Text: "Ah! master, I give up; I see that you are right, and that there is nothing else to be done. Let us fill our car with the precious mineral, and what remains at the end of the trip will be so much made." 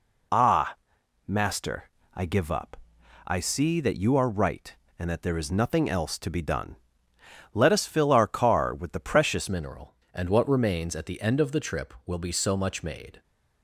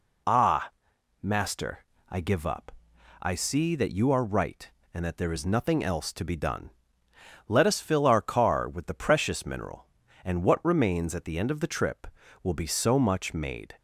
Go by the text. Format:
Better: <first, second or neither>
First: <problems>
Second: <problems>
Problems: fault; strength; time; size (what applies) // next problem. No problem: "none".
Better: second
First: changes voice at "mineral"; from 9.4 s on; 3.8 s long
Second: none